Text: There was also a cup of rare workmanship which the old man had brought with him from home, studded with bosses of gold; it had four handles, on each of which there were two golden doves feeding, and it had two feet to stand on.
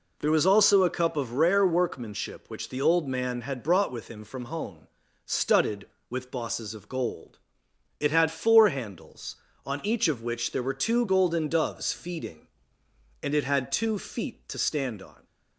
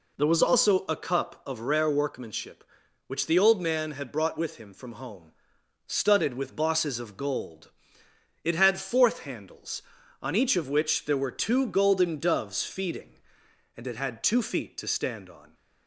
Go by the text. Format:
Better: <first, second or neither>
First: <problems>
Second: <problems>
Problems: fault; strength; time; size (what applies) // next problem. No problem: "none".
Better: first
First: none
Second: says "fourth" for "four"; at 8.7 s